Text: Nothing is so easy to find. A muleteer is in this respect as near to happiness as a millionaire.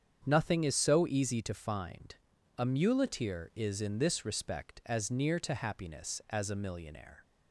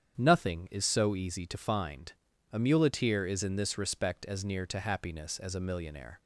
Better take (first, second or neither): neither